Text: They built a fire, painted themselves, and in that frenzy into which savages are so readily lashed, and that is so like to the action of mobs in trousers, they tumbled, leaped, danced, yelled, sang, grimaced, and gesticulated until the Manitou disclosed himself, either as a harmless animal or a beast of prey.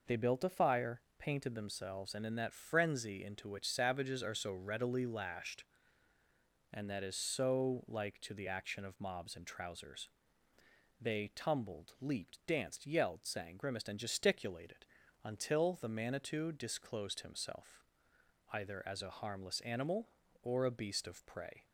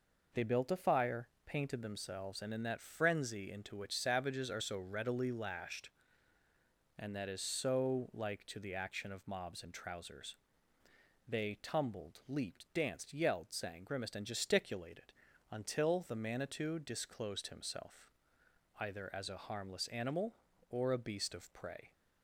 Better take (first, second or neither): neither